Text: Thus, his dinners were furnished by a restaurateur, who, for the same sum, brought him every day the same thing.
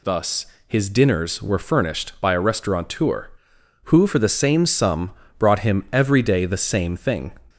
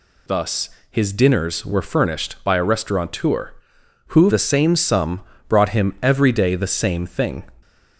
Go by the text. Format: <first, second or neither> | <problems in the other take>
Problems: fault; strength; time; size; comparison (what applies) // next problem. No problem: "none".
first | skips "for"; at 4.2 s